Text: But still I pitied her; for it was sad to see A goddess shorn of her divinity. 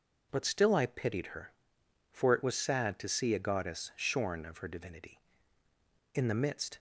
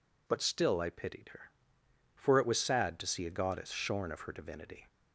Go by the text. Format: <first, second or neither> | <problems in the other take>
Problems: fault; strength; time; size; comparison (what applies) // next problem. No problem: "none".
second | goes on to say "In the midst"; noticeable; from 6.1 s on; 0.64 s long